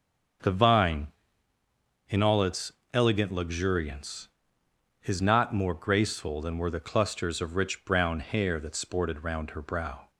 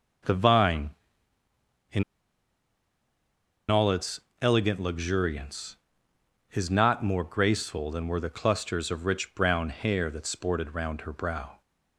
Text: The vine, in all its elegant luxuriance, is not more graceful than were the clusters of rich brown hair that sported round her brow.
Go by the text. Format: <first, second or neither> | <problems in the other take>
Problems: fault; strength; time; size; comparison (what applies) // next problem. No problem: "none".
first | starts louder than the rest; until 3.9 s; 7 dB; also in the first // pauses between "in" and "all"; strong; at 2.0 s; 1.6 s long // pauses between "its" and "elegant"; slight; at 4.2 s; 0.22 s long; slight in the first